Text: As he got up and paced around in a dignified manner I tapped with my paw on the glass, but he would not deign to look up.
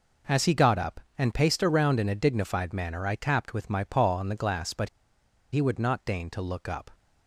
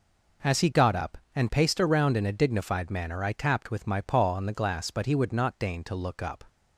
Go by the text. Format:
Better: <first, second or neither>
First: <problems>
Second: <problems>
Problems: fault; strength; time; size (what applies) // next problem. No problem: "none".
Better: second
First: pauses between "but" and "he"; noticeable; at 4.8 s; 0.64 s long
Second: none